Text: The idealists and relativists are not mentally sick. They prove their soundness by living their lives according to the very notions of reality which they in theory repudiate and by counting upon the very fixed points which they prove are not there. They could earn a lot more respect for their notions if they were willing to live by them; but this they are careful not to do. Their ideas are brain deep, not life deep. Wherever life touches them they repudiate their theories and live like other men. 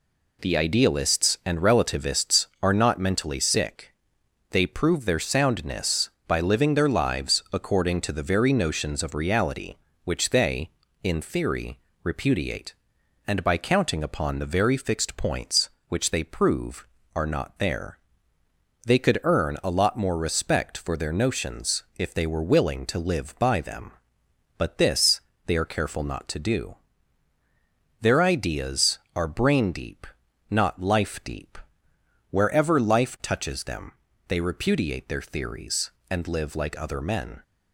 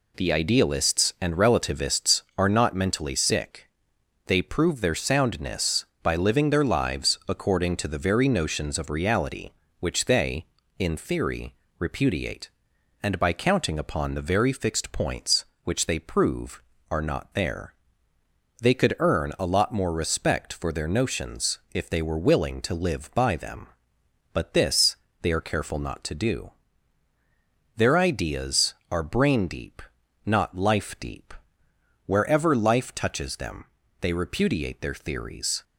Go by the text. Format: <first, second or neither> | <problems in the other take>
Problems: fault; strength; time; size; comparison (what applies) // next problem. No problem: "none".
first | pauses between "theory" and "repudiate"; slight; at 11.5 s; 0.24 s long; slight in the first // pauses between "this" and "they"; slight; at 24.9 s; 0.26 s long; slight in the first // pauses between "them" and "they"; slight; at 33.6 s; 0.34 s long; slight in the first // stops before "and live like other men"; at 35.6 s